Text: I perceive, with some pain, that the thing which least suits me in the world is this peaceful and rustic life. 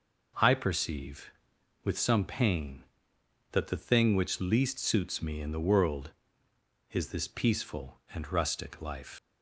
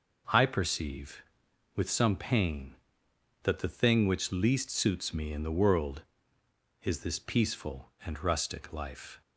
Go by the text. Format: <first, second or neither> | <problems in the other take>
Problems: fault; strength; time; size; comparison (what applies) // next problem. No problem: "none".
second | leaves "life" unfinished; at 9.1 s; 110 ms